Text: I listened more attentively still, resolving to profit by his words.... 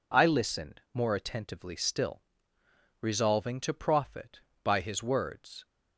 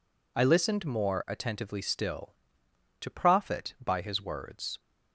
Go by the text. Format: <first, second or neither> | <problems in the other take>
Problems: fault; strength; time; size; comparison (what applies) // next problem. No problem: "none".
first | skips "resolving"; at 2.6 s